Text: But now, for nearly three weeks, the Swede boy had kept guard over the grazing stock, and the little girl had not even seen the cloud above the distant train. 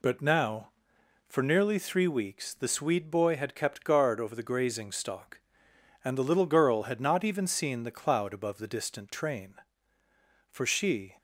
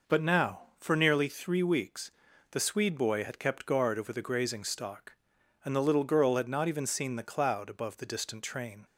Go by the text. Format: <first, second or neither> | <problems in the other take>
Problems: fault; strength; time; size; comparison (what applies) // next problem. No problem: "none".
second | goes on to say "For she"; noticeable; from 10.5 s on; 0.66 s long